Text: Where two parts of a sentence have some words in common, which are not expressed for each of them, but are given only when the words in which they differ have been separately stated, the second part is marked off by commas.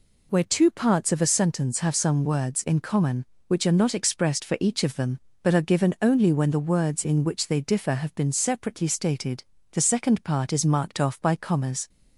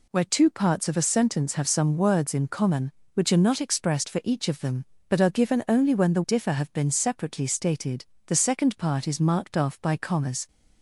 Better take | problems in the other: first | skips "words in which they"; at 6.2 s

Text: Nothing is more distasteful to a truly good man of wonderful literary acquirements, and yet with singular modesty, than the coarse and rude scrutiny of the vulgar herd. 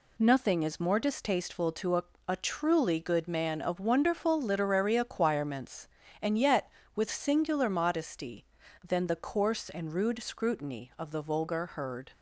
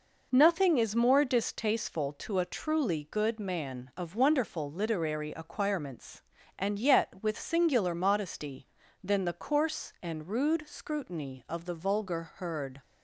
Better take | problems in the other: second | says "a" twice; at 2.2 s

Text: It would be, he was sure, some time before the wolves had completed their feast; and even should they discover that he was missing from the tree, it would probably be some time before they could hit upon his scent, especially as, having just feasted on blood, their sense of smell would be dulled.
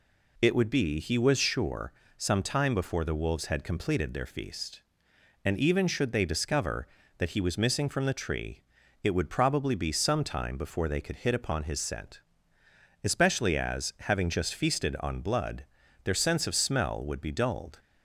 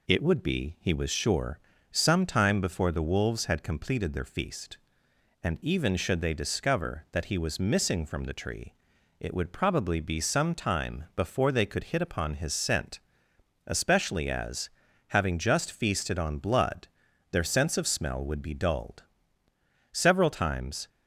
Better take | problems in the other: first | goes on to say "Several times"; noticeable; from 19.9 s on; 0.96 s long

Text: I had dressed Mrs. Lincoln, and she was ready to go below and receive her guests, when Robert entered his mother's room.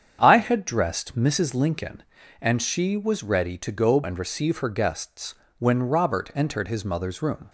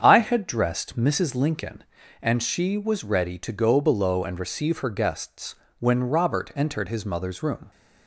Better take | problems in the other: second | starts louder than the rest; strong; until 1.2 s; 8 dB; strong in the second // skips "below"; at 4.0 s

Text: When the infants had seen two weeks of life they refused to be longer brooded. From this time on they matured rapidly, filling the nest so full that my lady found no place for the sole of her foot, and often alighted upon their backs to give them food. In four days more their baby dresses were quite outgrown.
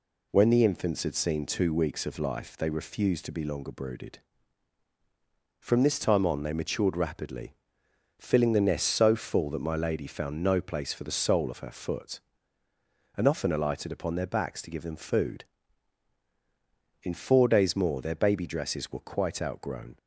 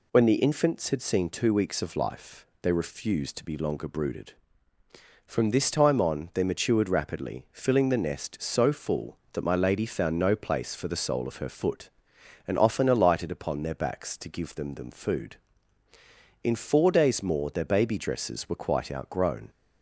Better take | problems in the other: first | pauses between "life" and "they"; slight; at 2.4 s; 0.16 s long // says "them" twice; at 14.7 s

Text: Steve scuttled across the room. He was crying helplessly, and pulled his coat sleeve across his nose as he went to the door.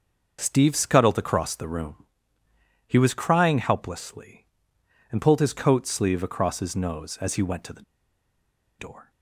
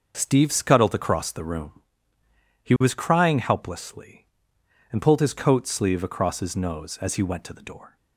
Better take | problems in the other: second | starts louder than the rest; noticeable; until 1.4 s; 6 dB; also in the second // pauses between "the" and "door"; noticeable; at 7.8 s; 0.97 s long

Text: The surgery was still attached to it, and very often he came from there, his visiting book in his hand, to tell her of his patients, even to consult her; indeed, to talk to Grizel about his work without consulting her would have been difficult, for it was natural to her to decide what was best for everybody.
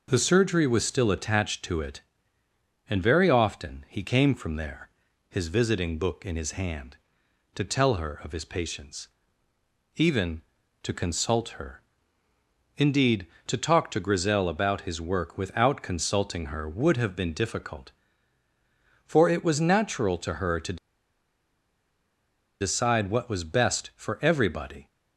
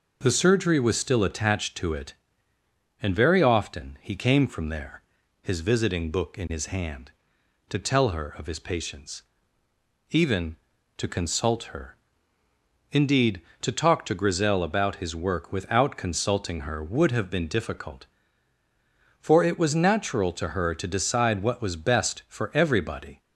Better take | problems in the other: second | pauses between "to" and "decide"; strong; at 20.7 s; 1.8 s long

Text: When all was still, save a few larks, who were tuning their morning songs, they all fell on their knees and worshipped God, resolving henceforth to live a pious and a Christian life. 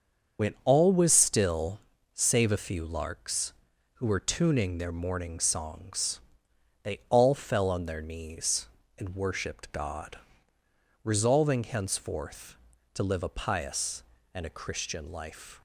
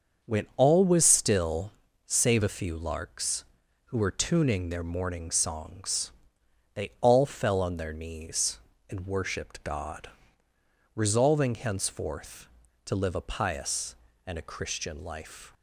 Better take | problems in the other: second | loses the start of "When"; at 0.3 s; 75 ms // starts louder than the rest; until 1.5 s; 6.5 dB; also in the second

